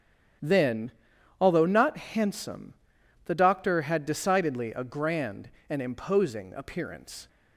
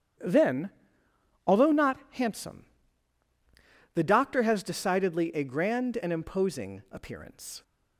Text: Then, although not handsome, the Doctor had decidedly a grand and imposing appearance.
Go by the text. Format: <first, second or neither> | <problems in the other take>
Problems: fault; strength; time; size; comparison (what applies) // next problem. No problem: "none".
first | starts louder than the rest; strong; until 1.9 s; 9.5 dB; strong in the first // says "has" for "had"; at 4.4 s